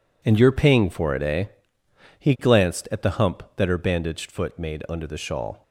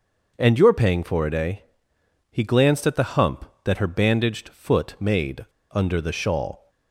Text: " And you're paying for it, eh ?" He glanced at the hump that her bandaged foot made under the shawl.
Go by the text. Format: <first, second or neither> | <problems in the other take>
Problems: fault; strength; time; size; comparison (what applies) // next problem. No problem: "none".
first | pauses between "made" and "under"; slight; at 5.4 s; 0.26 s long